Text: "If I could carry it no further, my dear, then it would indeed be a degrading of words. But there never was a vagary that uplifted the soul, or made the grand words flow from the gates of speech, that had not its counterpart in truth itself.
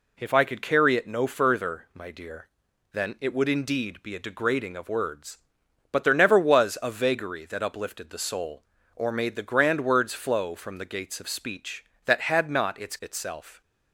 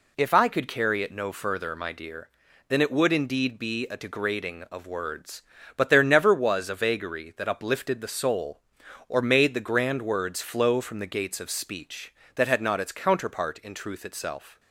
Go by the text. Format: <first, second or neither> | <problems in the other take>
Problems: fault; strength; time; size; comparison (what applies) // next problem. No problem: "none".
second | skips "counterpart in truth"; at 12.9 s